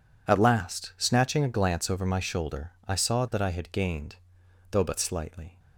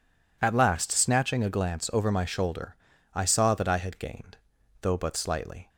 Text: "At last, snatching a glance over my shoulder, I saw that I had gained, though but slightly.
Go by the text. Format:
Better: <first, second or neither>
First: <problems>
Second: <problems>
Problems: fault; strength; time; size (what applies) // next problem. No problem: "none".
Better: neither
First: none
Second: none